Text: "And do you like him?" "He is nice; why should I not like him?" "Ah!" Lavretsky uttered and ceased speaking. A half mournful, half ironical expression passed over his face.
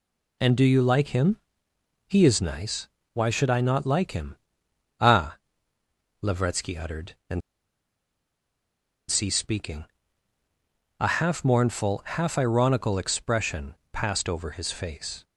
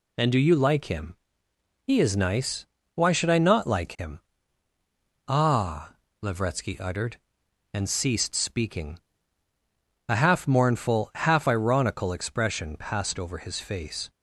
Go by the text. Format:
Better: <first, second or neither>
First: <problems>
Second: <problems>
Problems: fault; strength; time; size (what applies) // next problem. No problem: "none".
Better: second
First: pauses between "and" and "ceased"; strong; at 7.4 s; 1.6 s long // pauses between "expression" and "passed"; slight; at 13.7 s; 0.16 s long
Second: none